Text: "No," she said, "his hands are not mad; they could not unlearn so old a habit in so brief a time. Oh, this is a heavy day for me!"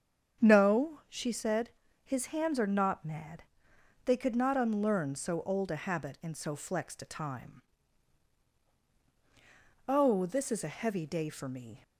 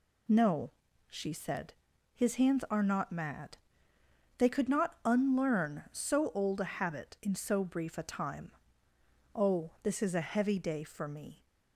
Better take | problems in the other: second | starts louder than the rest; strong; until 1.4 s; 7.5 dB // says "flexed" for "brief"; at 6.5 s

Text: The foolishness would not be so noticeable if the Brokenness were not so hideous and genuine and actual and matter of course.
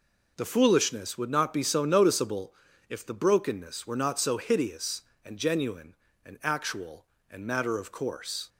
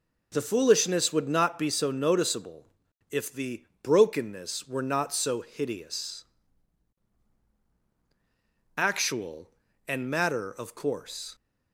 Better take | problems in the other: first | pauses between "noticeable" and "if"; noticeable; at 2.6 s; 0.46 s long; slight in the first // pauses between "the" and "Brokenness"; slight; at 3.6 s; 0.20 s long // skips "and genuine and"; at 7.4 s

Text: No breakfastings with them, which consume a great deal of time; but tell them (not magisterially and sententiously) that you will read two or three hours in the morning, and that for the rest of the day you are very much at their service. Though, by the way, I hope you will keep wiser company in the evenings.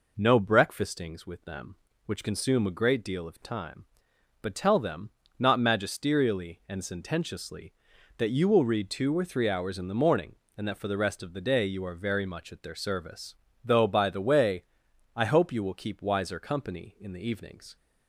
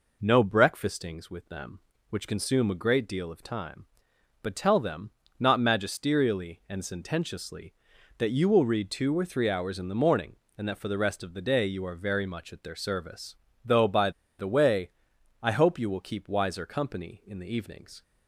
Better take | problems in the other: first | pauses between "by" and "the"; slight; at 14.1 s; 0.28 s long

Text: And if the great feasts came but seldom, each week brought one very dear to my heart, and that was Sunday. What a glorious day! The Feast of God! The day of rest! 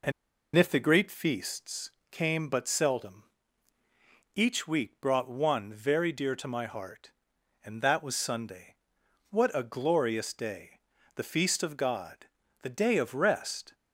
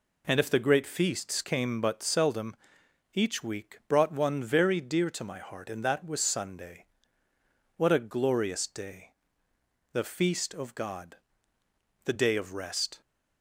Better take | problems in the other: second | pauses between "And" and "if"; at 0.1 s; 0.43 s long // pauses between "feasts" and "came"; slight; at 1.8 s; 0.22 s long

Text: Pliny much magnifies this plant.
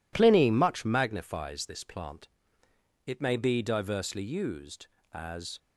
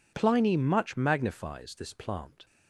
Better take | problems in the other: second | goes on to say "It may be diversely used as"; strong; from 3.0 s on; 2.5 s long

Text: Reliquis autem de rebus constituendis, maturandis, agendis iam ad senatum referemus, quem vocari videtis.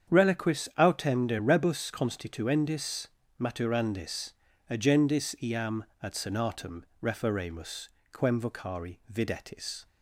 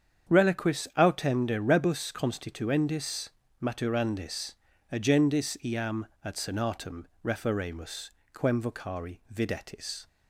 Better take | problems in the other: neither | starts louder than the rest; strong; the same in both // pauses between "iam" and "ad"; slight; the same in both // pauses between "senatum" and "referemus"; slight; the same in both

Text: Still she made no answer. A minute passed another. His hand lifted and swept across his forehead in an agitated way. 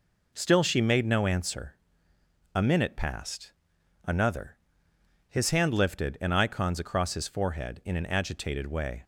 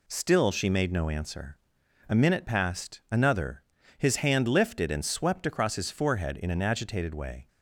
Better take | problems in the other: second | pauses between "passed" and "another"; noticeable; at 3.5 s; 0.54 s long // says "icons" for "swept"; at 6.3 s

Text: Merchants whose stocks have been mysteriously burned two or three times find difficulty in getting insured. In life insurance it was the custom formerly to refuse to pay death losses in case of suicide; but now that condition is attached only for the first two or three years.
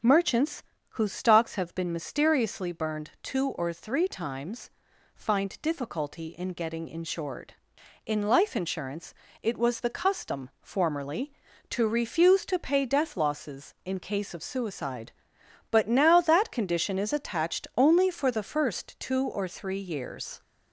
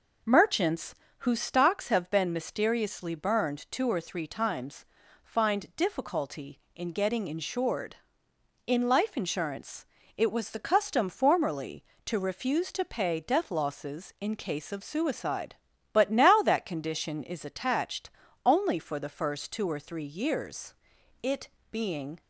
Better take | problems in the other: first | pauses between "Merchants" and "whose"; slight; at 0.9 s; 0.24 s long; slight in the first // pauses between "times" and "find"; at 4.8 s; 0.40 s long; noticeable in the first // pauses between "insurance" and "it"; slight; at 9.8 s; 0.30 s long; slight in the first // pauses between "attached" and "only"; slight; at 18.0 s; 0.36 s long // goes on to say "It being"; noticeable; from 21.2 s on; 1.0 s long

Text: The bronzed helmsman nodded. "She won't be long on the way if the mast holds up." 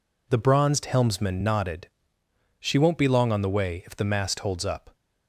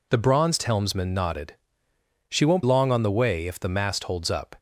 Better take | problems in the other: first | skips "be"; at 2.6 s

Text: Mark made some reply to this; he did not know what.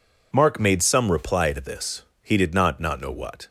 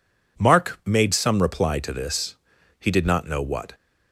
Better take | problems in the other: second | says "not" twice; at 2.7 s

